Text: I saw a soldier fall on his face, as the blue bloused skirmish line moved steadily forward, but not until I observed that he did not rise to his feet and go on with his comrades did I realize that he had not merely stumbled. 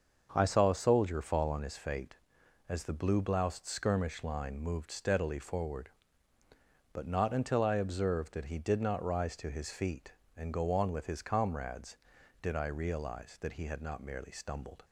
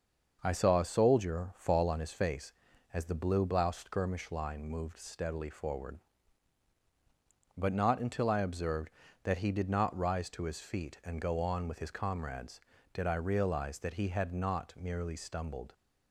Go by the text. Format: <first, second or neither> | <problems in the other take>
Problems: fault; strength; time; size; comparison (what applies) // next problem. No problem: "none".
second | starts louder than the rest; until 1.3 s; 6.5 dB; noticeable in the second // says "fate" for "face"; at 1.7 s